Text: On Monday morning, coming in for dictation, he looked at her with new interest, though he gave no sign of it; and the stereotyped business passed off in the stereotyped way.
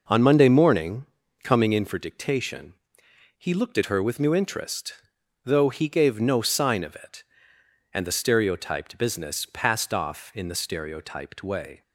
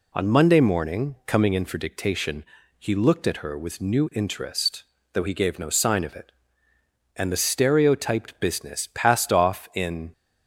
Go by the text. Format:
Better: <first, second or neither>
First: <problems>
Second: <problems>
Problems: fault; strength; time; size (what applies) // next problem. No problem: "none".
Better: first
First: none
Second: stops before "the stereotyped way"; at 10.1 s